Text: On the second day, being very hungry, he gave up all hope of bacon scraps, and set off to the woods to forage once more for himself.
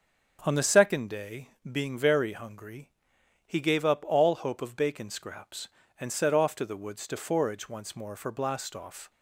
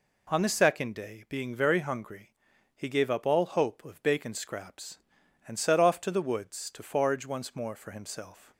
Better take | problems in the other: second | starts louder than the rest; until 1.4 s; 6.5 dB // says "blastoff" for "himself"; at 8.3 s

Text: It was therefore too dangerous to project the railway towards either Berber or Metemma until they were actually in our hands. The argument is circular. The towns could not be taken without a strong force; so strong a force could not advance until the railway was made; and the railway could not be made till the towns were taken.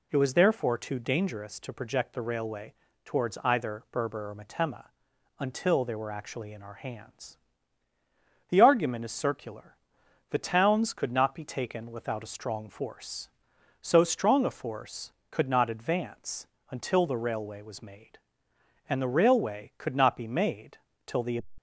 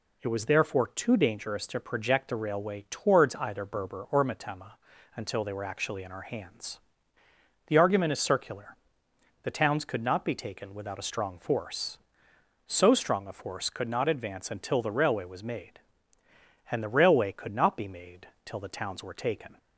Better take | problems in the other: second | pauses between "railway" and "towards"; slight; at 2.7 s; 0.32 s long // pauses between "Metemma" and "until"; noticeable; at 4.8 s; 0.50 s long; also in the second // pauses between "advance" and "until"; slight; at 16.4 s; 0.24 s long // pauses between "made" and "till"; slight; at 20.7 s; 0.26 s long; slight in the second // stops before "towns were taken"; at 21.5 s

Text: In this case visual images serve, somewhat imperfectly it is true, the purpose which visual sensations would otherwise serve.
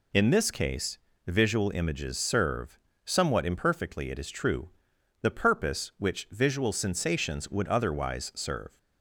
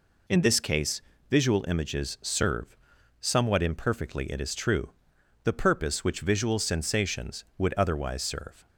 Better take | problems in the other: neither | pauses between "case" and "visual"; slight; the same in both

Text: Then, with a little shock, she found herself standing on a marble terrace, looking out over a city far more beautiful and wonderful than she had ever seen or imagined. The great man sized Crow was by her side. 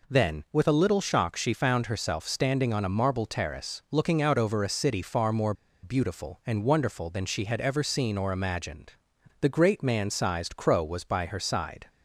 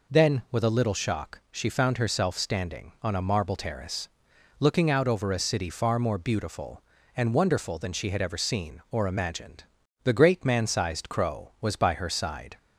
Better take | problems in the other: second | pauses between "more" and "beautiful"; slight; at 5.5 s; 0.28 s long

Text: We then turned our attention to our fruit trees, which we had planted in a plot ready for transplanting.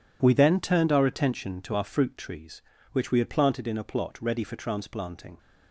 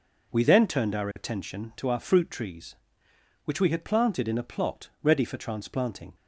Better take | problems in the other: neither | none

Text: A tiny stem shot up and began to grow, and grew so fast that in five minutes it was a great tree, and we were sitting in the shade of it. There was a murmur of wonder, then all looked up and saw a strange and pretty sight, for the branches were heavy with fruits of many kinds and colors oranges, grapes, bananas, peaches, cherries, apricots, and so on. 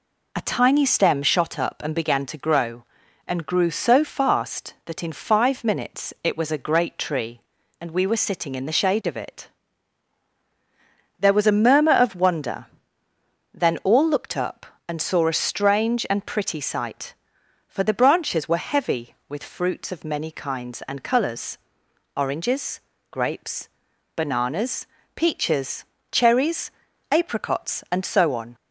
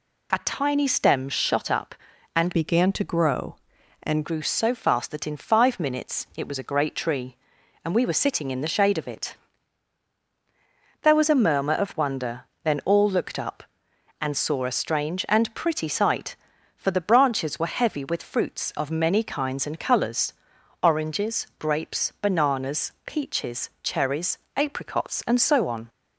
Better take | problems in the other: first | changes voice from "began" to "and"; from 2.5 to 4.2 s; 1.7 s long // pauses between "colors" and "oranges"; noticeable; at 20.3 s; 0.50 s long; noticeable in the first

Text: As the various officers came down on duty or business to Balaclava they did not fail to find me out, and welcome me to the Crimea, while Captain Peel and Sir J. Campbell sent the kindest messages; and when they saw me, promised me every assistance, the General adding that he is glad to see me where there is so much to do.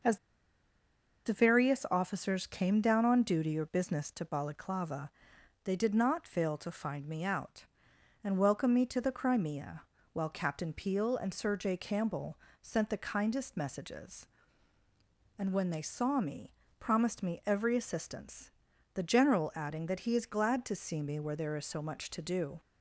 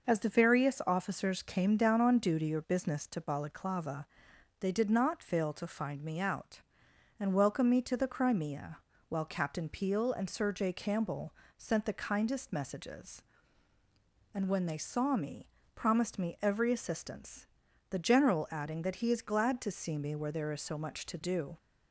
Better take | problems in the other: second | pauses between "As" and "the"; at 0.1 s; 1.0 s long // pauses between "Balaclava" and "they"; noticeable; at 5.0 s; 0.54 s long; noticeable in the second // pauses between "Campbell" and "sent"; slight; at 12.3 s; 0.24 s long; slight in the second

